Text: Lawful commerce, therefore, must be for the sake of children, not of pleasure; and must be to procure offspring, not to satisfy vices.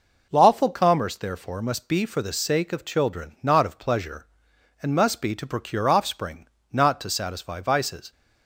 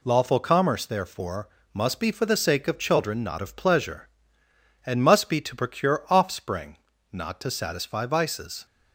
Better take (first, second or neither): neither